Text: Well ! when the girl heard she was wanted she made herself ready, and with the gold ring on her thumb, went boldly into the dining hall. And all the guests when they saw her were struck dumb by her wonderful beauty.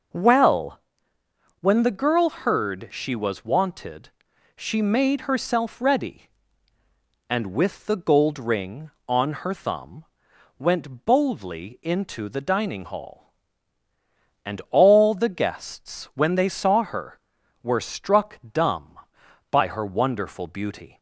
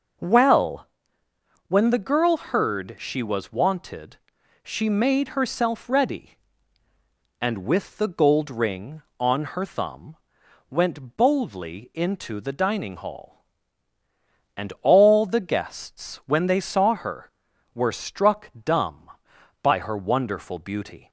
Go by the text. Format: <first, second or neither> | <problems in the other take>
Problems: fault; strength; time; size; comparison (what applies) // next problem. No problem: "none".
neither | pauses between "wanted" and "she"; noticeable; the same in both // pauses between "struck" and "dumb"; slight; the same in both